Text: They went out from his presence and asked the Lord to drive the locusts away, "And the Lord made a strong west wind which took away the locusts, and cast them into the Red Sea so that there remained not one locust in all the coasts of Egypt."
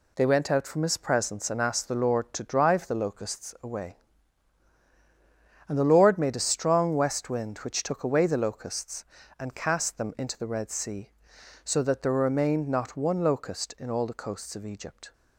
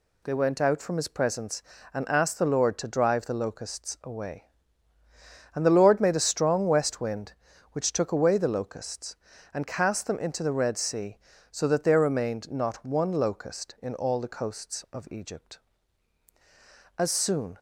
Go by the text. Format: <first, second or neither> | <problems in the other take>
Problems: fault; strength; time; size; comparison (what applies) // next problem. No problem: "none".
first | goes on to say "As soon"; noticeable; from 16.9 s on; 0.62 s long